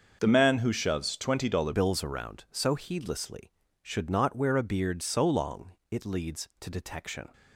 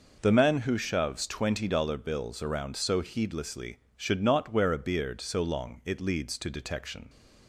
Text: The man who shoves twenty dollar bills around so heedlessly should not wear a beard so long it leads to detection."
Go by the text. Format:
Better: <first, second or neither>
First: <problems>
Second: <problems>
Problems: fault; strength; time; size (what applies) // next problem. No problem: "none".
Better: second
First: starts louder than the rest; until 1.2 s; 6.5 dB // changes voice at "bills"; from 1.7 s on; 5.6 s long // pauses between "long" and "it"; slight; at 5.7 s; 0.18 s long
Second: none